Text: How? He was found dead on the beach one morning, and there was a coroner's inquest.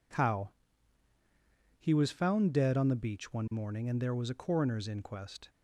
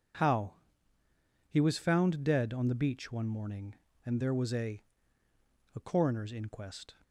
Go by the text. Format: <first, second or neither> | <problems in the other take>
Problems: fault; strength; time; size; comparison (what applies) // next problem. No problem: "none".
first | says "a" twice; at 5.7 s